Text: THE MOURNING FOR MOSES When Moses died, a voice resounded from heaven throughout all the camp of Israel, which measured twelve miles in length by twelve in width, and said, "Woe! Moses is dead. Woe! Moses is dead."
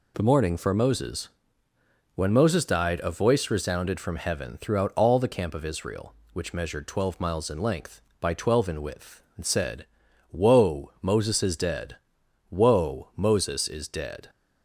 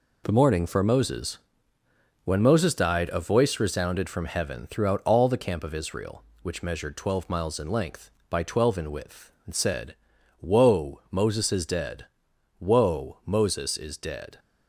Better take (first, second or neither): first